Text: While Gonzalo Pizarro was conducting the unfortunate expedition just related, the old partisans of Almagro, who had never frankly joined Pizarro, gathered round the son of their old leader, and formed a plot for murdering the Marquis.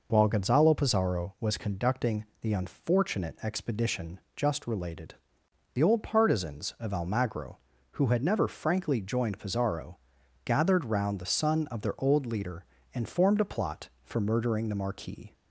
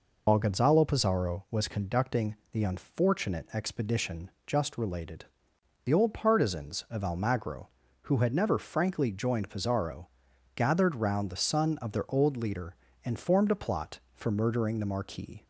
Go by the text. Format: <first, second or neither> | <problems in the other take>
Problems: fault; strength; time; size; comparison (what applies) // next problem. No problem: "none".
first | loses the start of "While"; at 0.2 s; 65 ms // pauses between "conducting" and "the"; slight; at 2.3 s; 0.16 s long; slight in the first // pauses between "expedition" and "just"; slight; at 4.2 s; 0.16 s long; slight in the first